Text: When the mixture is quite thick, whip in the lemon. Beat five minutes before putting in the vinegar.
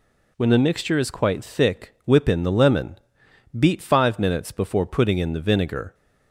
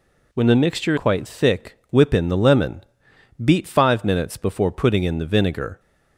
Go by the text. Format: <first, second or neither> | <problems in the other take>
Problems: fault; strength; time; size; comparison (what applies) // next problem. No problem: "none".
first | skips "is"; at 0.9 s